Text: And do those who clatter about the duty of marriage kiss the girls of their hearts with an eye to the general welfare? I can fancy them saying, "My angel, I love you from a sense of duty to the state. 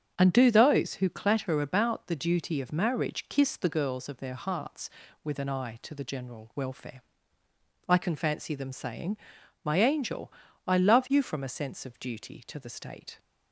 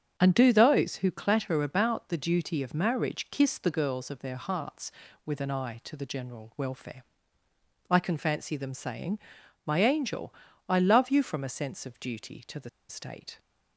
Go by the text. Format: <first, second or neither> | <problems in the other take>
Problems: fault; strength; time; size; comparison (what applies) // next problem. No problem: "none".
first | starts louder than the rest; strong; until 1.1 s; 7.5 dB; strong in the first // pauses between "the" and "state"; slight; at 12.6 s; 0.20 s long